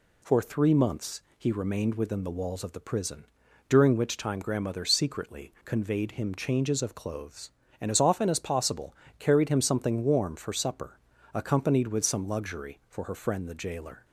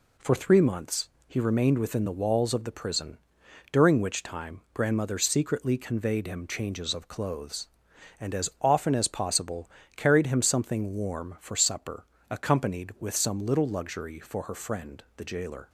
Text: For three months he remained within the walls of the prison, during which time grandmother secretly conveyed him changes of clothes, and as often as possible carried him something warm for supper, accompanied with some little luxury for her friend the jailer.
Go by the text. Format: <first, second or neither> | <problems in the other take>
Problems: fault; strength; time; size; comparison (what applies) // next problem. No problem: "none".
second | pauses between "months" and "he"; slight; at 1.2 s; 0.16 s long; slight in the second // pauses between "possible" and "carried"; slight; at 8.9 s; 0.24 s long; slight in the second // skips "little"; at 12.2 s